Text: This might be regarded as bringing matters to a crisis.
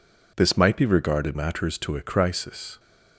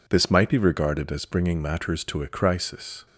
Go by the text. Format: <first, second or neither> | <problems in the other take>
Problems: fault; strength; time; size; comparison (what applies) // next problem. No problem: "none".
second | skips "as bringing"; at 1.3 s